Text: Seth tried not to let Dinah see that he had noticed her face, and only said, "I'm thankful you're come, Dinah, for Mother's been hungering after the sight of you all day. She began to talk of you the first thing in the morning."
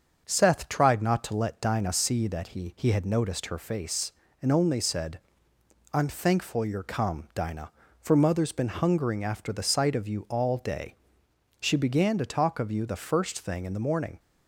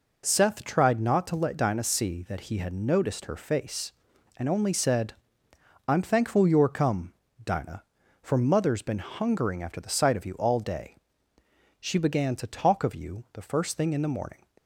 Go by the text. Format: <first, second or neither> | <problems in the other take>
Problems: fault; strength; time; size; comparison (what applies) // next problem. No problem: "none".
second | starts louder than the rest; until 1.2 s; 6.5 dB // says "he" twice; at 2.7 s